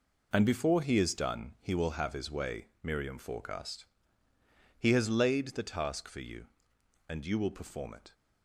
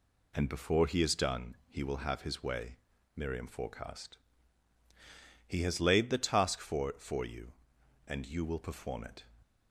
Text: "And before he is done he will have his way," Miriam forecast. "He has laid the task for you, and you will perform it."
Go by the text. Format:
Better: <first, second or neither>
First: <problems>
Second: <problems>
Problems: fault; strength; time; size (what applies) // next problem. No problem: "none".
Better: first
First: none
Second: says "for" twice; at 6.9 s